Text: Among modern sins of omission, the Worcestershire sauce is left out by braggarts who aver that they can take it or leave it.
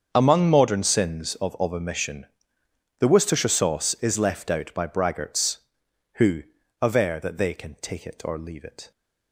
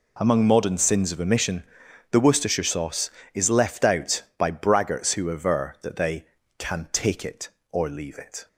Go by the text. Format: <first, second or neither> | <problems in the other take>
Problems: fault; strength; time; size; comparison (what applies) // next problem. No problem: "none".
second | starts louder than the rest; until 1.1 s; 7 dB // says "of" twice; at 1.5 s // pauses between "who" and "aver"; at 6.4 s; 0.40 s long